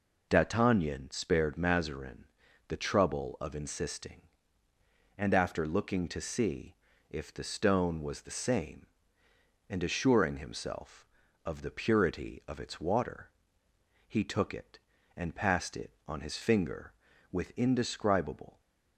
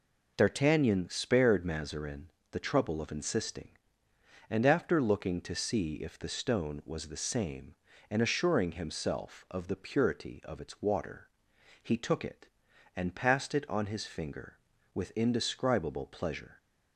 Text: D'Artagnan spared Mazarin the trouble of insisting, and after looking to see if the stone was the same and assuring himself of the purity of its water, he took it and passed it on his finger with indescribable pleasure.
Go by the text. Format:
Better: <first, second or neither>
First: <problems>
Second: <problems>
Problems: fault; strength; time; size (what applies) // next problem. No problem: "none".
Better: second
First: pauses between "Mazarin" and "the"; at 2.2 s; 0.42 s long // pauses between "see" and "if"; slight; at 6.7 s; 0.34 s long // stops before "pleasure"; at 18.5 s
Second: pauses between "Mazarin" and "the"; slight; at 2.3 s; 0.20 s long